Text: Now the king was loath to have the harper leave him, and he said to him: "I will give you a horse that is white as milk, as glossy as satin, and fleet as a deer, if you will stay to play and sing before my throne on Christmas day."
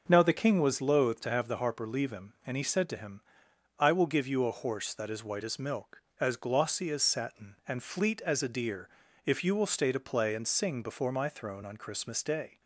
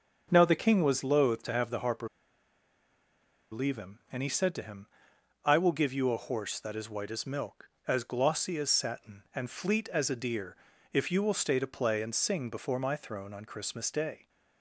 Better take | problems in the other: first | pauses between "harper" and "leave"; strong; at 2.0 s; 1.4 s long

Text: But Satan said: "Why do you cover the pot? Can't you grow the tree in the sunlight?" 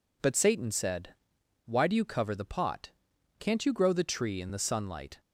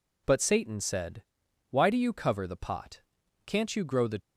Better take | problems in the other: first | stops before "tree in the sunlight"; at 4.2 s

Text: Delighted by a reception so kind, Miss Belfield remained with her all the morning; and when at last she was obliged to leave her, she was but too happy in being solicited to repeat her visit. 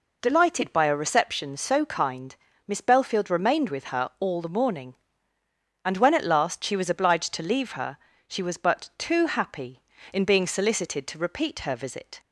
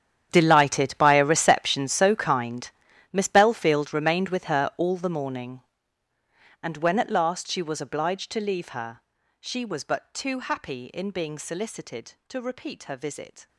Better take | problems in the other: first | gets quieter; strong; throughout; 18.5 dB

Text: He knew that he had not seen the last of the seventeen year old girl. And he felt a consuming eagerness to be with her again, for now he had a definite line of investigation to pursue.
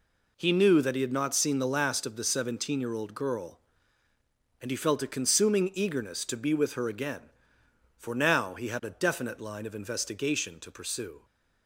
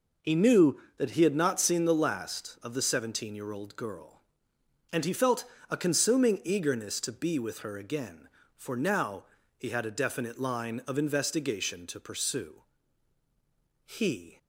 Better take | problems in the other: first | pauses between "felt" and "a"; slight; at 5.4 s; 0.26 s long // pauses between "now" and "he"; slight; at 9.2 s; 0.34 s long // goes on to say "He"; from 13.8 s on; 0.52 s long

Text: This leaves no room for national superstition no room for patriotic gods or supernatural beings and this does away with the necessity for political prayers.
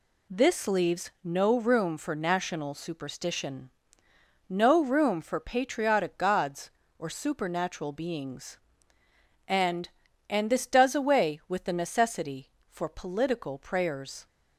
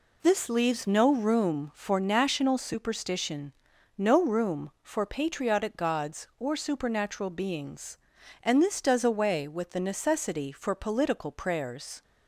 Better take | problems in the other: second | pauses between "superstition" and "no"; noticeable; at 3.6 s; 0.80 s long; also in the second // says "and" twice; at 10.2 s

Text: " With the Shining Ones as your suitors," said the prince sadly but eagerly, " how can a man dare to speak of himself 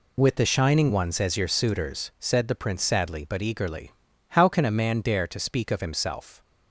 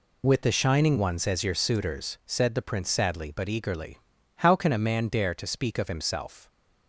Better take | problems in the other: neither | none

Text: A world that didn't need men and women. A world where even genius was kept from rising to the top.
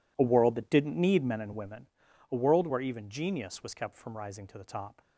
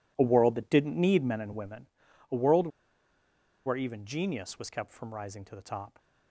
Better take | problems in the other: first | pauses between "world" and "where"; noticeable; at 2.6 s; 0.97 s long

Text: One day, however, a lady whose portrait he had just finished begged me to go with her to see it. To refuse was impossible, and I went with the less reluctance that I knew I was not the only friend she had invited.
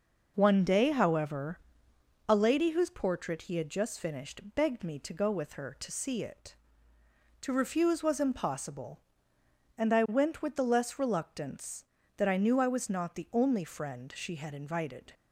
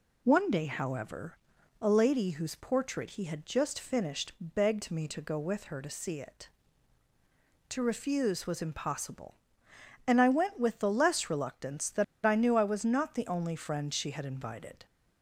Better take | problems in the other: first | pauses between "that" and "I"; slight; at 12.0 s; 0.20 s long

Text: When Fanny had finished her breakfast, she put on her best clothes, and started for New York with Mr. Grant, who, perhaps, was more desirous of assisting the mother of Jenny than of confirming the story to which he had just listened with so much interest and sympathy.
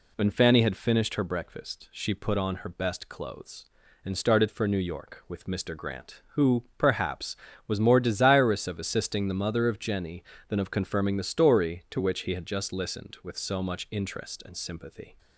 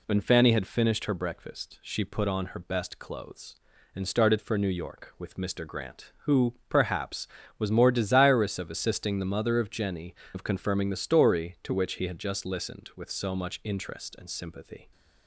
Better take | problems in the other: first | skips "than"; at 10.2 s

